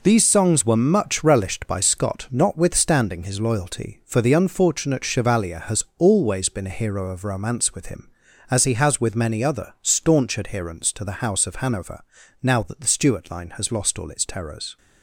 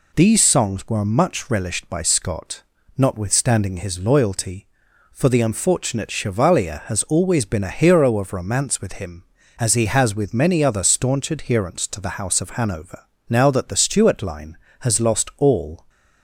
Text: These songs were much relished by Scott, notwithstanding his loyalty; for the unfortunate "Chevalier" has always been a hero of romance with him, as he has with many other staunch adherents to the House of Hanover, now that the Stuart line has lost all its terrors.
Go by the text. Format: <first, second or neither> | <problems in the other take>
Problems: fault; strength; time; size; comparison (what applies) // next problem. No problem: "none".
first | stops before "its terrors"; at 15.8 s